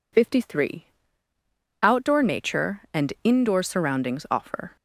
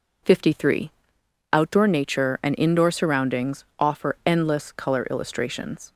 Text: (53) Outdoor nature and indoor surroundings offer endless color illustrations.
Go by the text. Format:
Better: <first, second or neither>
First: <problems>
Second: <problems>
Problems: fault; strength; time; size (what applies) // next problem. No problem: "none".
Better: second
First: stops before "endless color illustrations"; at 4.7 s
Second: none